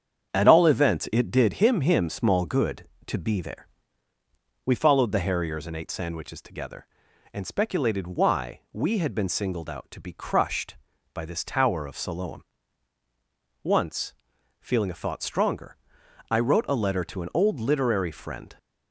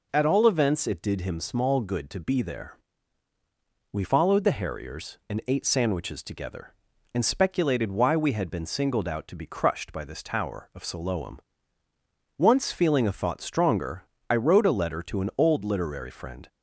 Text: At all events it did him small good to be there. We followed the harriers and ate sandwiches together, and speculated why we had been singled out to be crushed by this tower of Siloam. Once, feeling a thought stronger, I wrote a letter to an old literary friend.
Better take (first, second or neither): second